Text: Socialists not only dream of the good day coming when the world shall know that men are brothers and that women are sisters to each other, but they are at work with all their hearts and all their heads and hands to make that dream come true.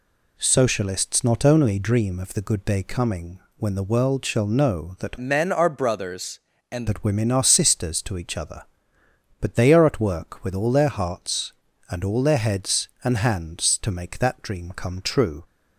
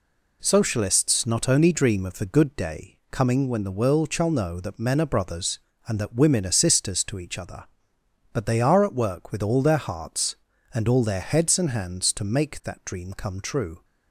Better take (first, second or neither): second